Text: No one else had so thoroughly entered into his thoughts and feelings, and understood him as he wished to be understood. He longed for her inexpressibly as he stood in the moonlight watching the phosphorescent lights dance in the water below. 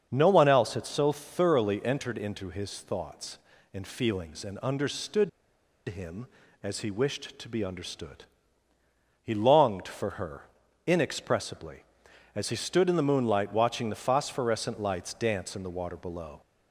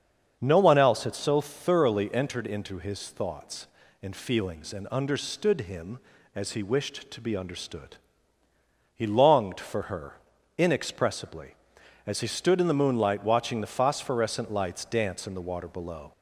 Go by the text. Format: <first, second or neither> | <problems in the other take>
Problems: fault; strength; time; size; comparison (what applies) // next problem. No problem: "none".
second | starts louder than the rest; strong; until 1.1 s; 7 dB; strong in the second // pauses between "understood" and "him"; noticeable; at 5.2 s; 0.58 s long // pauses between "her" and "inexpressibly"; at 10.4 s; 0.40 s long; also in the second